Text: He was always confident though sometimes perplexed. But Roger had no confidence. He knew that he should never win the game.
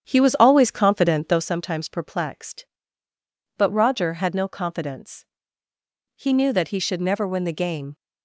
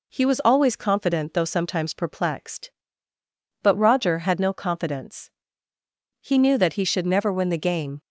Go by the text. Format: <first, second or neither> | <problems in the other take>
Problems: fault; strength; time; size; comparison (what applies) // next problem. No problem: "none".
second | starts louder than the rest; strong; until 1.4 s; 9 dB